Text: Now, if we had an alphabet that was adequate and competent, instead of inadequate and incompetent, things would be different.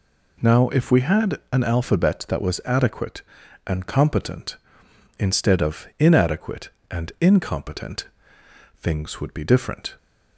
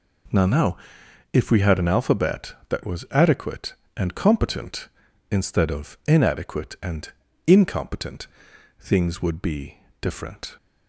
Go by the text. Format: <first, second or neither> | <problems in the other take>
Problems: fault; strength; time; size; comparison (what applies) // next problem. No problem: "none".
first | says "Now" twice; at 0.4 s // pauses between "and" and "incompetent"; at 7.0 s; 0.38 s long // pauses between "be" and "different"; slight; at 9.7 s; 0.22 s long